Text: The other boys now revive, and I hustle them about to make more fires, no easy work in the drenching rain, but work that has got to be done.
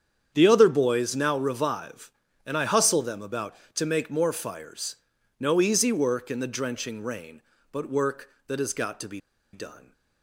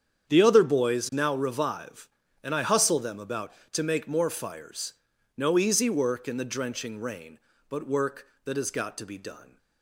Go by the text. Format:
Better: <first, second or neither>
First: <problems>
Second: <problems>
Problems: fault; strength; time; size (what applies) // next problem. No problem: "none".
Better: second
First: starts louder than the rest; strong; until 1.3 s; 8 dB // pauses between "be" and "done"; slight; at 9.2 s; 0.32 s long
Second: starts louder than the rest; strong; until 1.3 s; 8 dB